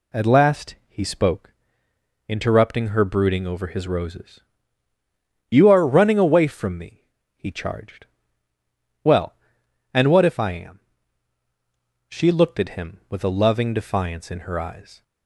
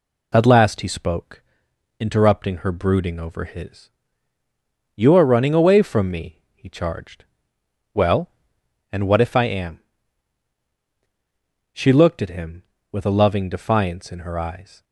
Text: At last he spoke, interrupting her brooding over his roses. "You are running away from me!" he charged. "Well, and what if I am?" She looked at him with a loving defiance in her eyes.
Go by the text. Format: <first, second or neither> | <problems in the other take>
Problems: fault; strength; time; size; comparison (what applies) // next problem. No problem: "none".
first | skips "roses"; at 4.4 s